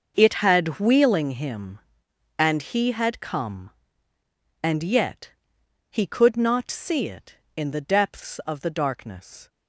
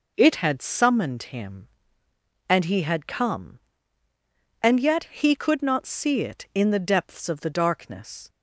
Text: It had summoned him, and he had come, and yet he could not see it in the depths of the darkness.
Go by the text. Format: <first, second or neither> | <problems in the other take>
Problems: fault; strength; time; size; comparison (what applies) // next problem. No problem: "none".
second | starts louder than the rest; noticeable; until 1.1 s; 6 dB // says "wheeling" for "summoned"; at 0.7 s // pauses between "yet" and "he"; noticeable; at 5.3 s; 0.60 s long